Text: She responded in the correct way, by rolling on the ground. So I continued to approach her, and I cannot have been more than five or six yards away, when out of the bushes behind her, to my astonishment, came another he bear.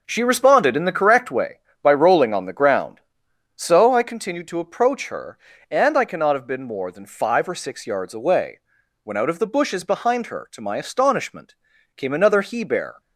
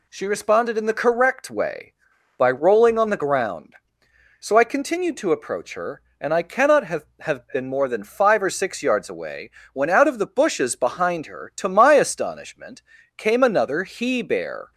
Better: first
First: none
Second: says "have" twice; at 7.1 s

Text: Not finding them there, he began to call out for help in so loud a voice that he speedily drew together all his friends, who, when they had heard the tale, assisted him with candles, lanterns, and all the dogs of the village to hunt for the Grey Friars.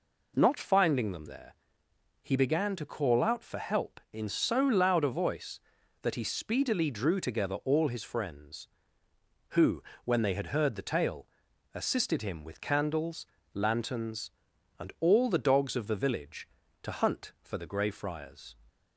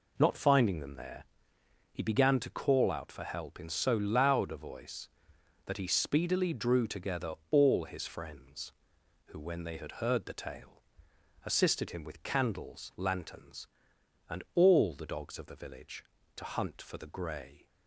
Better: first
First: none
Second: pauses between "together" and "all"; slight; at 7.3 s; 0.18 s long // stops before "Friars"; at 17.6 s

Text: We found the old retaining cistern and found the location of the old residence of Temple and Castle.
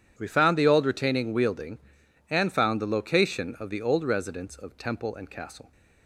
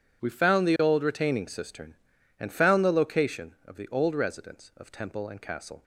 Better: second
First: starts louder than the rest; strong; until 1.1 s; 9.5 dB // says "wielding" for "cistern"; at 1.3 s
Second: none

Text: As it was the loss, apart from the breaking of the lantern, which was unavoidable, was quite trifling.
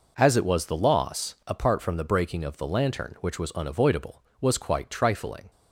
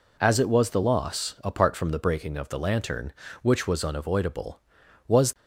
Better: first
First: none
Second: stops before "quite trifling"; at 5.3 s

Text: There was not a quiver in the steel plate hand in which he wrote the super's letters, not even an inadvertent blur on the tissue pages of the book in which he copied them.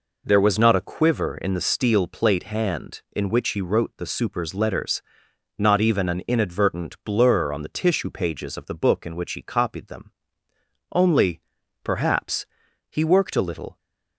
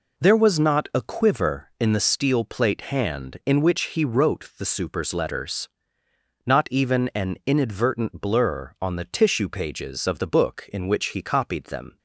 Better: second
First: goes on to say "Only perhaps he worked a little"; strong; from 10.9 s on; 2.8 s long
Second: none

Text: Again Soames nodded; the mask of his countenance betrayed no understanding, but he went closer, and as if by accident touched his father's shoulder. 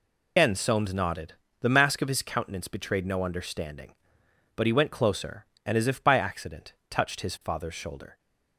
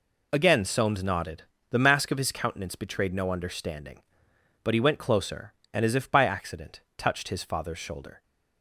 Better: second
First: loses the start of "Again"; at 0.3 s; 135 ms // pauses between "accident" and "touched"; slight; at 6.7 s; 0.16 s long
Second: pauses between "accident" and "touched"; slight; at 6.8 s; 0.16 s long

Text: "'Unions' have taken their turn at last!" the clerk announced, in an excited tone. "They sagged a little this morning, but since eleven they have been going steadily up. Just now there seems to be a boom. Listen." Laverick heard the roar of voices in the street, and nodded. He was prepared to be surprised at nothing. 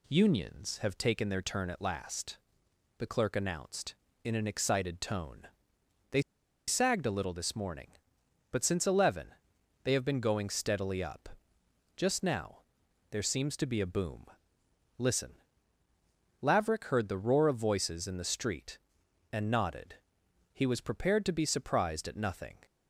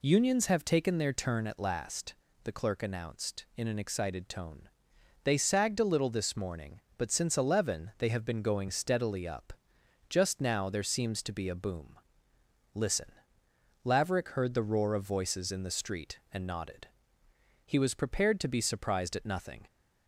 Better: second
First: pauses between "They" and "sagged"; noticeable; at 6.2 s; 0.46 s long // pauses between "eleven" and "they"; noticeable; at 9.2 s; 0.56 s long // pauses between "now" and "there"; noticeable; at 12.6 s; 0.48 s long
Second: none

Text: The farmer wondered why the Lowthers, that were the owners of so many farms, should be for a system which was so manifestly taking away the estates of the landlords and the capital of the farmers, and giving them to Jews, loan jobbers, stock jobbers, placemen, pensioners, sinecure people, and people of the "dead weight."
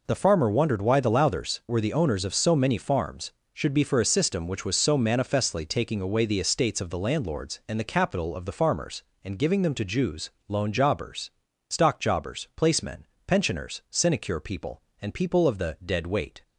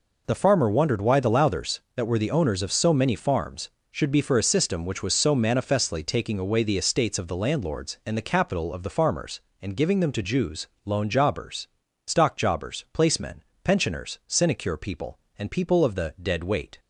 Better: second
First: skips "that"; at 1.6 s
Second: none

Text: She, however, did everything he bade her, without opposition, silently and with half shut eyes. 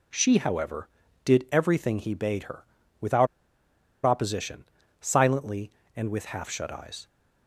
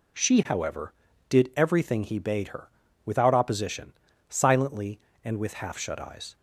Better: second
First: pauses between "without" and "opposition"; noticeable; at 3.2 s; 0.78 s long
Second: none

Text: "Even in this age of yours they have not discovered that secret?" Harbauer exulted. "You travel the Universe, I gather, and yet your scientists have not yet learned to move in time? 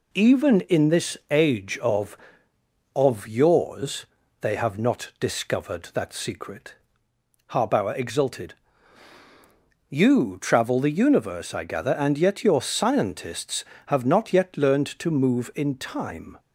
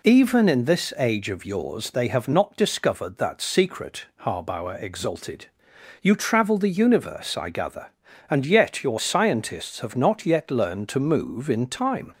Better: second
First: says "of" twice; at 2.9 s // pauses between "yours" and "they"; slight; at 4.0 s; 0.36 s long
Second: none

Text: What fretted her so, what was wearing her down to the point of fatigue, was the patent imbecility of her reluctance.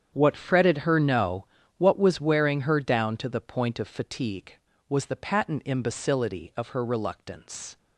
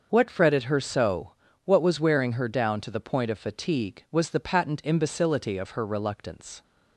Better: second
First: starts louder than the rest; strong; until 1.1 s; 8.5 dB // says "no" for "so"; at 0.9 s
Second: starts louder than the rest; until 1.1 s; 6 dB

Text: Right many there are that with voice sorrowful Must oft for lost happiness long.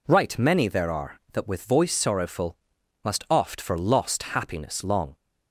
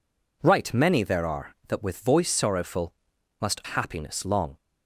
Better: first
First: pauses between "sorrowful" and "Must"; noticeable; at 2.5 s; 0.48 s long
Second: pauses between "sorrowful" and "Must"; noticeable; at 2.9 s; 0.48 s long // skips "oft for lost"; at 3.6 s

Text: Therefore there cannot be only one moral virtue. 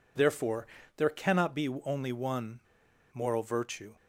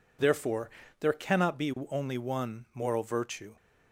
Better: second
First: pauses between "Therefore" and "there"; slight; at 0.6 s; 0.30 s long // pauses between "one" and "moral"; noticeable; at 2.6 s; 0.55 s long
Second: pauses between "Therefore" and "there"; slight; at 0.6 s; 0.30 s long

